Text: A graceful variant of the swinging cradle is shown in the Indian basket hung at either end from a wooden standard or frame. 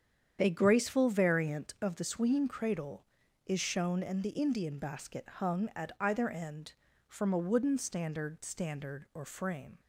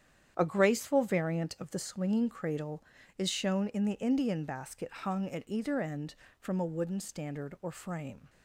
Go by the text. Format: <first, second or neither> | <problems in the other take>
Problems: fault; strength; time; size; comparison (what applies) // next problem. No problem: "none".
second | starts louder than the rest; strong; until 1.4 s; 8.5 dB; strong in the second // says "standard" twice; at 8.4 s